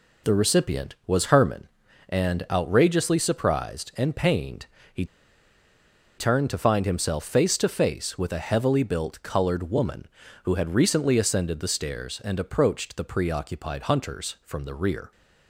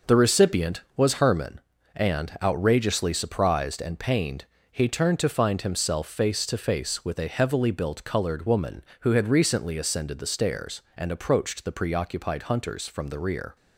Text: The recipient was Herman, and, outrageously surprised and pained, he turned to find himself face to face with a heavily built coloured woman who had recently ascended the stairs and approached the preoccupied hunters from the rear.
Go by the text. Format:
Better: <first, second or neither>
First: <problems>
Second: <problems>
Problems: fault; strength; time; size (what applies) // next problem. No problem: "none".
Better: second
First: pauses between "he" and "turned"; at 5.0 s; 1.1 s long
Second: none